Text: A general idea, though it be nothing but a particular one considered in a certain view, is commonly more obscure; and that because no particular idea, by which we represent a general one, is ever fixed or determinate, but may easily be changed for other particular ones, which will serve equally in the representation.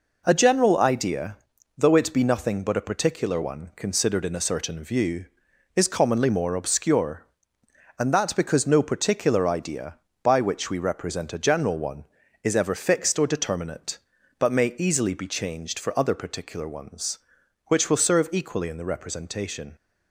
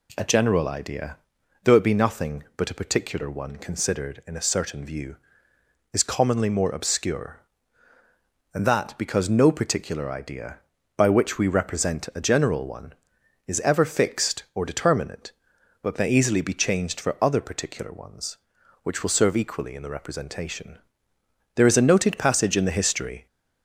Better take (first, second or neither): first